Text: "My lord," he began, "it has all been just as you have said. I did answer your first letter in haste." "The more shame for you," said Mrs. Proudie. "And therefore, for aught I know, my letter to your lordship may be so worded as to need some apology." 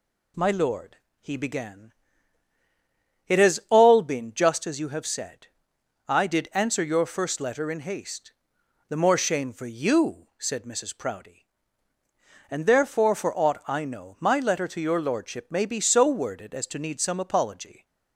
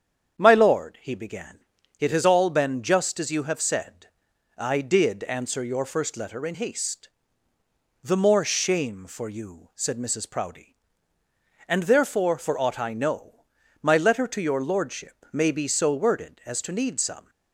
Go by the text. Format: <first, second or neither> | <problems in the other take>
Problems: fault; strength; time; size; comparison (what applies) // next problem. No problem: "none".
first | starts louder than the rest; strong; until 1.4 s; 8 dB // stops before "apology"; at 17.2 s